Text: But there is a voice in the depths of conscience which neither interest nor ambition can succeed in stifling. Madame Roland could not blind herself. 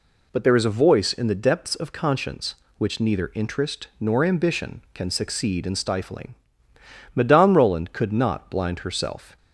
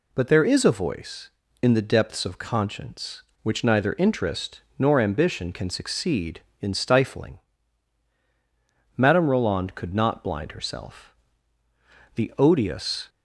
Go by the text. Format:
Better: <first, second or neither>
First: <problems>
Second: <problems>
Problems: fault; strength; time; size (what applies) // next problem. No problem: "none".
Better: first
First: none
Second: pauses between "interest" and "nor"; slight; at 4.6 s; 0.16 s long // goes on to say "The odious"; noticeable; from 12.1 s on; 0.94 s long